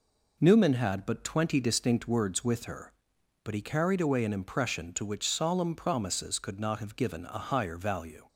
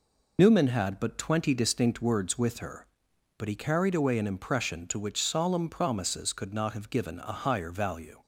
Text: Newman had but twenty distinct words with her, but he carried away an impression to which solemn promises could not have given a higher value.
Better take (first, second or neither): first